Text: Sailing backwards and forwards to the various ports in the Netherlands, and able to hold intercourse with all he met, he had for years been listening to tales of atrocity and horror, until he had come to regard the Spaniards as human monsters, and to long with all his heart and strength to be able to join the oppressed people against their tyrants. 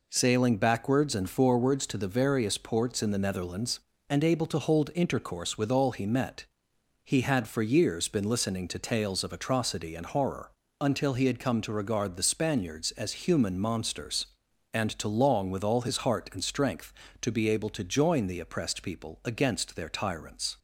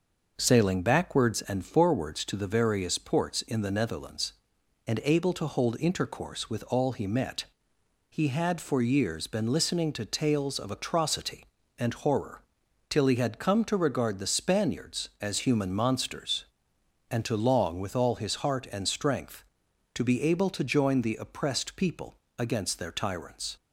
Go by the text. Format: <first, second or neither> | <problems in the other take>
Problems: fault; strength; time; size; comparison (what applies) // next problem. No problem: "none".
first | says "till" for "until"; at 12.8 s // pauses between "people" and "against"; slight; at 22.1 s; 0.20 s long